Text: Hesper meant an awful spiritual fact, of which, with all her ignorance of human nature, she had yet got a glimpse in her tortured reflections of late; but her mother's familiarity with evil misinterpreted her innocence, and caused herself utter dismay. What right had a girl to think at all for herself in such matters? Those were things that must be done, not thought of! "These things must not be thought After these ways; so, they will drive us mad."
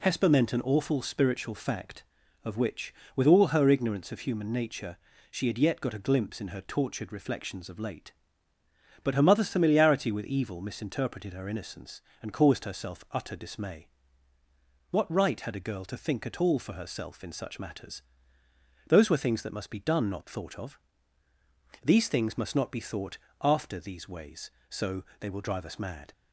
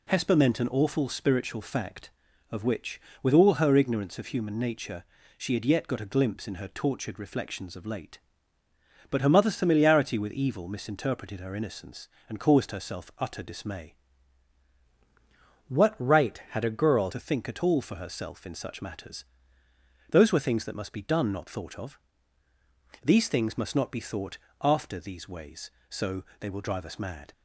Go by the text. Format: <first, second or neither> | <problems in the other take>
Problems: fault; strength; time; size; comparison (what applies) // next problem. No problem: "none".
first | changes voice from "What" to "girl"; from 15.6 to 17.0 s; 1.4 s long // pauses between "thought" and "After"; slight; at 24.3 s; 0.24 s long; slight in the first